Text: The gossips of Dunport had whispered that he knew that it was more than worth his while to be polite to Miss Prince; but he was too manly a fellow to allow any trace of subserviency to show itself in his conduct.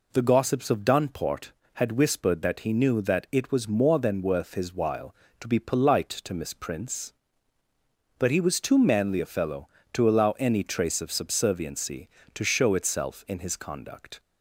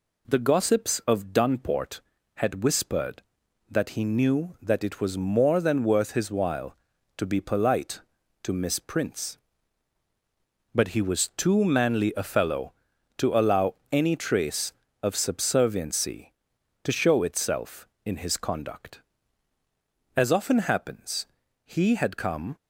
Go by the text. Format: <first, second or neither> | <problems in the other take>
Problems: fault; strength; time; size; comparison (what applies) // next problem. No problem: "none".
first | pauses between "allow" and "any"; slight; at 13.7 s; 0.16 s long // goes on to say "As often happens he had come"; strong; from 20.1 s on; 2.3 s long